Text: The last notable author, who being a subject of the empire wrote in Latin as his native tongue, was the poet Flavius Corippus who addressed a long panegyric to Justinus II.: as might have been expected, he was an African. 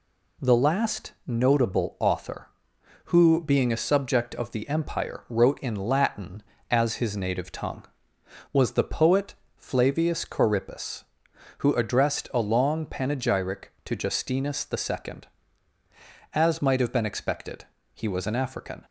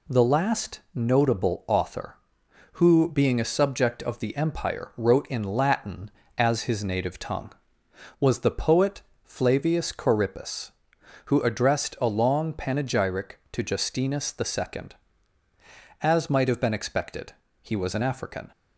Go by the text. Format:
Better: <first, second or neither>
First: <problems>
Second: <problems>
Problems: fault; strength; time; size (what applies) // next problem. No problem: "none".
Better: neither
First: pauses between "last" and "notable"; slight; at 1.1 s; 0.16 s long // pauses between "poet" and "Flavius"; slight; at 9.3 s; 0.24 s long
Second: pauses between "last" and "notable"; slight; at 0.7 s; 0.16 s long // pauses between "poet" and "Flavius"; slight; at 9.0 s; 0.24 s long